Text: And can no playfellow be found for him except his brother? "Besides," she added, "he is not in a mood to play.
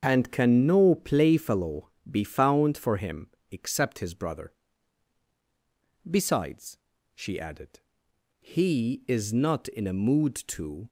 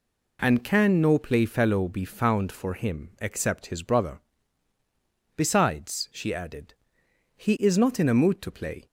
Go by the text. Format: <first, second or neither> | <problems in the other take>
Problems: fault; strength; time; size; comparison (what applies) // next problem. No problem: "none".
second | starts louder than the rest; until 1.0 s; 7 dB // pauses between "playfellow" and "be"; slight; at 1.8 s; 0.22 s long // pauses between "him" and "except"; slight; at 3.2 s; 0.22 s long // stops before "play"; at 10.8 s